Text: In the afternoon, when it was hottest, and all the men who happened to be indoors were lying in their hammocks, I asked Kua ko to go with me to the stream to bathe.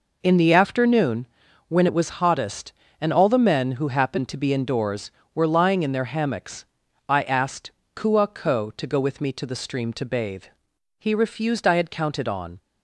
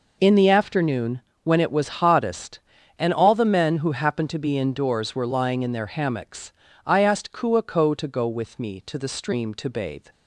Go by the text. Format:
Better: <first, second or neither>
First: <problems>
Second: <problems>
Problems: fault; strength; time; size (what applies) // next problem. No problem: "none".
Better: second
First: pauses between "asked" and "Kua"; slight; at 7.7 s; 0.24 s long // goes on to say "He refused I had counted on"; from 10.9 s on; 1.6 s long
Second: none